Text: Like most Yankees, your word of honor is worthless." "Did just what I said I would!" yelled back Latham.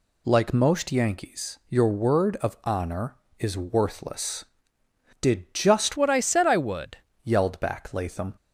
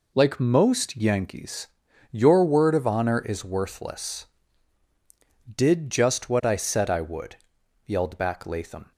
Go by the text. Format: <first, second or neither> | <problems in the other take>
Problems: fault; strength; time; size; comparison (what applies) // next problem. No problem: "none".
second | changes voice from "what" to "would"; from 5.9 to 6.9 s; 1.0 s long